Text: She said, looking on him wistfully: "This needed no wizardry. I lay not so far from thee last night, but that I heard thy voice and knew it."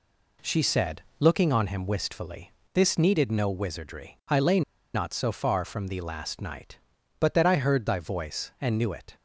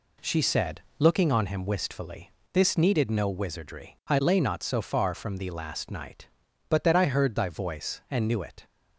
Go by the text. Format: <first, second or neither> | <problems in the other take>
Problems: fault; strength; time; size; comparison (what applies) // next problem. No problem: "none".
second | pauses between "lay" and "not"; slight; at 4.6 s; 0.33 s long